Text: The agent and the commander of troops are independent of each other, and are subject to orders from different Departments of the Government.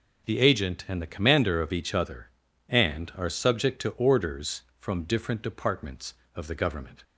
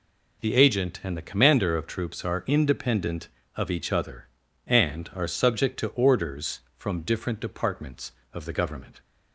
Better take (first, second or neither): second